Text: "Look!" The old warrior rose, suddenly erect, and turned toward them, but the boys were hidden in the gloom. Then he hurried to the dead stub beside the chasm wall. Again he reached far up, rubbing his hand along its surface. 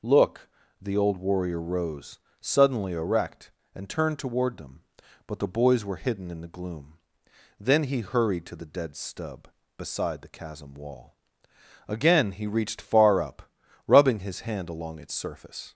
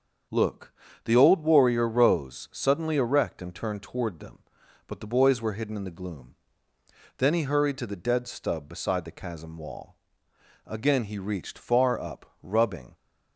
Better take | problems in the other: first | starts louder than the rest; strong; until 1.6 s; 7 dB // stops before "his hand along its surface"; at 12.9 s

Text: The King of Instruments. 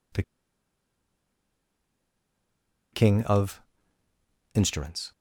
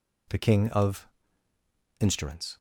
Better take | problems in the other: second | pauses between "The" and "King"; strong; at 0.2 s; 2.7 s long // pauses between "of" and "Instruments"; noticeable; at 3.6 s; 0.92 s long; noticeable in the second

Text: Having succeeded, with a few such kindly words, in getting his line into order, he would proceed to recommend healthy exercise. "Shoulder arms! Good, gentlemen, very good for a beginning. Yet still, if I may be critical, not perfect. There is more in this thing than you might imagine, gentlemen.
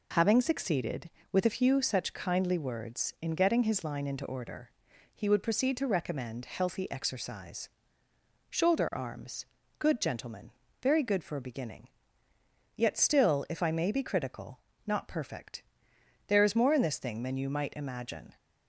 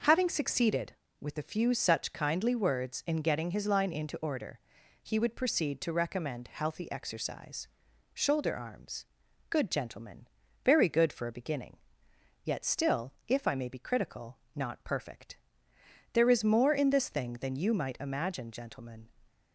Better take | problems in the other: second | stops before "gentlemen"; at 18.3 s

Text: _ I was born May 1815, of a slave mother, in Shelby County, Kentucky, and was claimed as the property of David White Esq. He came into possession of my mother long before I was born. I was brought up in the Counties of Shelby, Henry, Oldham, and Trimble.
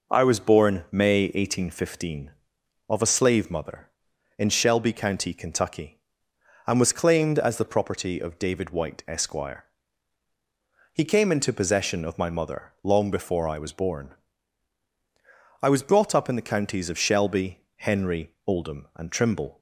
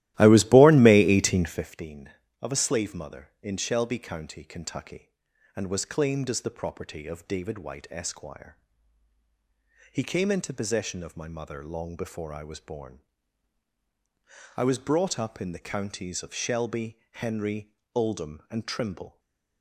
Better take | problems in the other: first | starts louder than the rest; strong; until 1.7 s; 15 dB // stays silent after the last word; slight; from 19.0 s on; 0.6 s long

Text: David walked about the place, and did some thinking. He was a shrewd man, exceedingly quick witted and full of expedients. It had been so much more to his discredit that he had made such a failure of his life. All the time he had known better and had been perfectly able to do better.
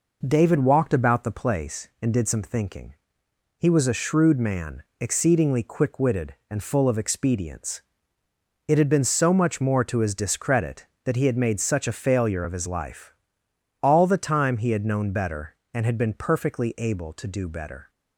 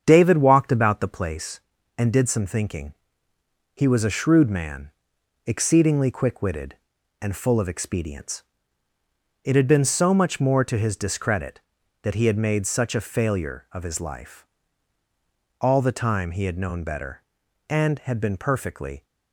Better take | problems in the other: first | starts louder than the rest; strong; until 1.0 s; 8 dB // stops before "able to do better"; at 19.0 s

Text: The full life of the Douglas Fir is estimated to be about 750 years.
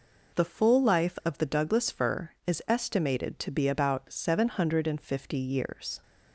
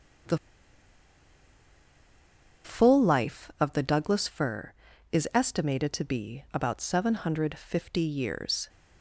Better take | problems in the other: first | starts louder than the rest; strong; until 3.6 s; 7.5 dB // pauses between "The" and "full"; strong; at 0.3 s; 2.2 s long

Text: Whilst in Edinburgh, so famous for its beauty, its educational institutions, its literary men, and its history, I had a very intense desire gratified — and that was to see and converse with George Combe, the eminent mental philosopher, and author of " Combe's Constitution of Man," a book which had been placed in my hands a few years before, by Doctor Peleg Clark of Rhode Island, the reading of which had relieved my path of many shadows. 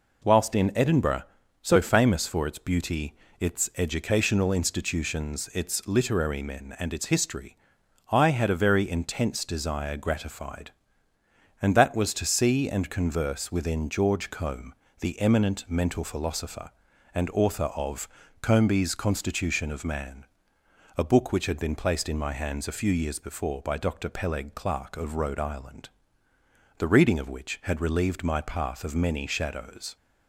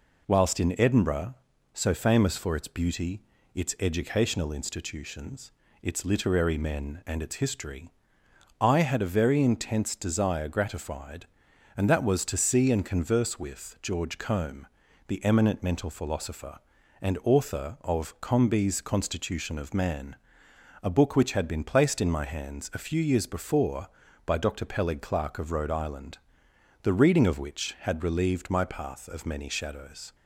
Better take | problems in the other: second | says "within" for "with"; at 13.4 s

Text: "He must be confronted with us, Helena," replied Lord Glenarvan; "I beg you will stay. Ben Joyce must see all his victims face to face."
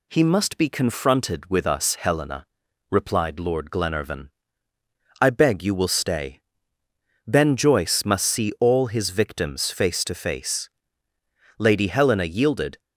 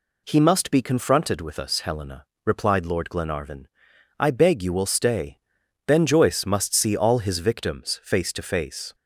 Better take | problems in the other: second | goes on to say "Lady Helena yielded"; noticeable; from 11.5 s on; 1.2 s long

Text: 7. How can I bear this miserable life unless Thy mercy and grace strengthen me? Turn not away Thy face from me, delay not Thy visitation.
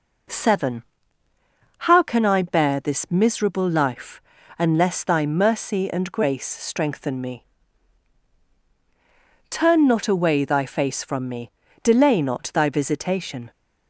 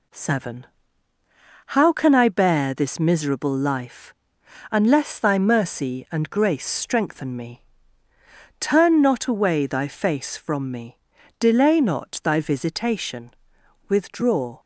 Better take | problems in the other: first | pauses between "life" and "unless"; noticeable; at 4.1 s; 0.58 s long; also in the first // goes on to say "Withdraw"; noticeable; from 13.8 s on; 0.72 s long

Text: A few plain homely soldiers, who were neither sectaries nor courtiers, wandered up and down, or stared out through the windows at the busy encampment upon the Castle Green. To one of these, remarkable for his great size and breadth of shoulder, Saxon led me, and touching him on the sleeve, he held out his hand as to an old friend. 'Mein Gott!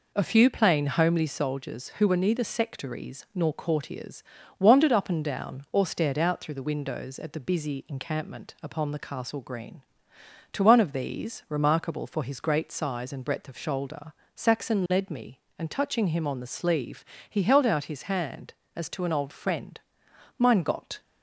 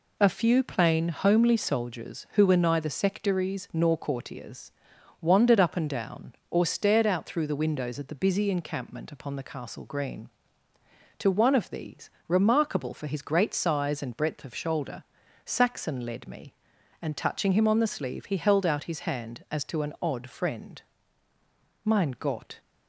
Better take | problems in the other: first | says "odd" for "old"; at 19.9 s

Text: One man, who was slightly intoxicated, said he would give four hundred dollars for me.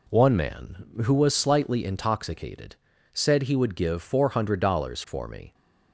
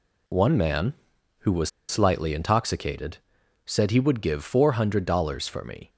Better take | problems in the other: first | pauses between "was" and "slightly"; slight; at 1.6 s; 0.20 s long

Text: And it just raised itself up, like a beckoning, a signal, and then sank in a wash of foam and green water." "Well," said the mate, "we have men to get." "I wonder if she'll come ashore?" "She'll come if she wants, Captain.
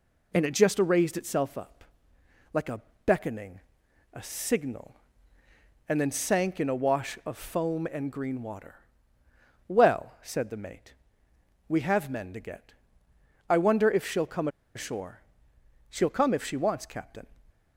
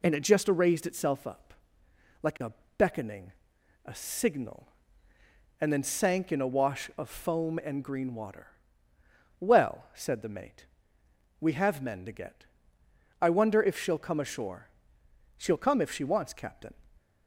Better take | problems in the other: second | pauses between "a" and "beckoning"; slight; at 2.7 s; 0.26 s long; slight in the second // pauses between "come" and "ashore"; slight; at 14.4 s; 0.27 s long

